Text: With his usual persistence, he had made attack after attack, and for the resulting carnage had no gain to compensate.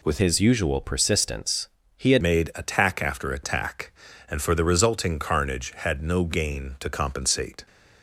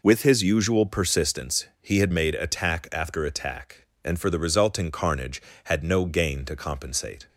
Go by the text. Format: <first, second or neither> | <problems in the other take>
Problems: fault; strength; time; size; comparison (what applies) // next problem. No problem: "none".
second | changes voice from "his" to "had"; from 0.1 to 2.2 s; 2.1 s long